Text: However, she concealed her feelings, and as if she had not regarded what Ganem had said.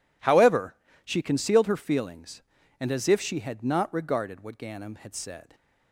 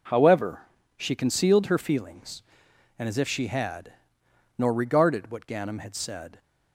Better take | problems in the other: first | says "nor" for "not"; at 4.5 s

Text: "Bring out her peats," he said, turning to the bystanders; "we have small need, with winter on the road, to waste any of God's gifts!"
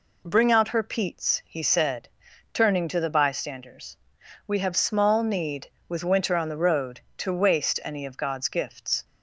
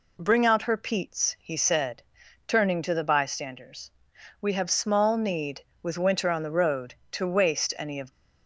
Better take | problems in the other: first | stops before "God's gifts"; at 8.1 s

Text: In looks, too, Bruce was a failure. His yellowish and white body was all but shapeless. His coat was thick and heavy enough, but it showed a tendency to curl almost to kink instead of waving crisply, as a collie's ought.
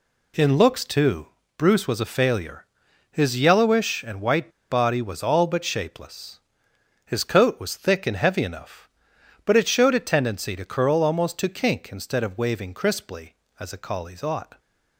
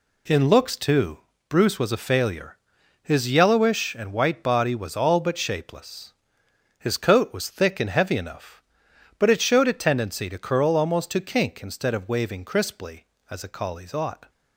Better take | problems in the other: second | pauses between "white" and "body"; slight; at 4.5 s; 0.19 s long

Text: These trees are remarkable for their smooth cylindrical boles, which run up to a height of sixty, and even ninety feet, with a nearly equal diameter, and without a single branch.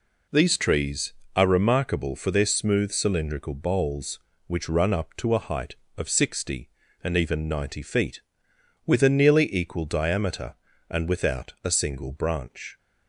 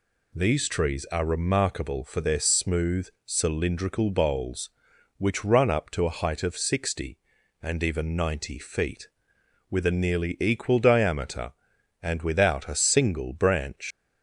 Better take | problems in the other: first | pauses between "smooth" and "cylindrical"; slight; at 3.0 s; 0.18 s long // leaves "branch" unfinished; at 13.9 s; 115 ms

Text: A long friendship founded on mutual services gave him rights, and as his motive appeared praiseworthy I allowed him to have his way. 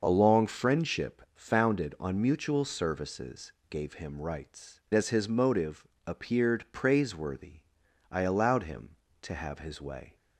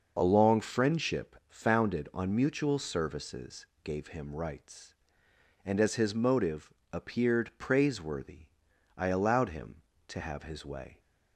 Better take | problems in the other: second | pauses between "services" and "gave"; slight; at 3.5 s; 0.16 s long; slight in the second // skips "and"; at 4.8 s // pauses between "motive" and "appeared"; slight; at 5.8 s; 0.18 s long; slight in the second // pauses between "praiseworthy" and "I"; noticeable; at 7.6 s; 0.50 s long; noticeable in the second

